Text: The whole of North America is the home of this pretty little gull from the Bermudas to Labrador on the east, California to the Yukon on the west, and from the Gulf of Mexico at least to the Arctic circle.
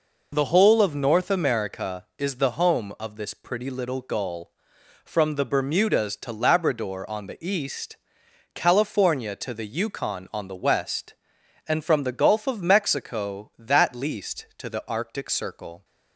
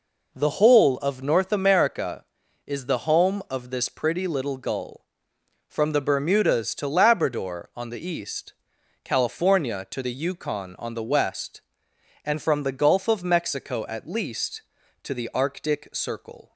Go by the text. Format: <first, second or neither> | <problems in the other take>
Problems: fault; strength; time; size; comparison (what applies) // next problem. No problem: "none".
second | says "that" for "at"; at 13.5 s